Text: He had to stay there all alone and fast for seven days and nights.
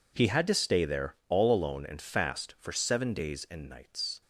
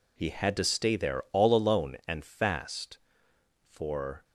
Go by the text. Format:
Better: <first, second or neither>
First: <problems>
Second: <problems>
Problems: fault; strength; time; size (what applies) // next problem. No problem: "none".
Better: first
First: none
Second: stops before "seven days and nights"; at 4.2 s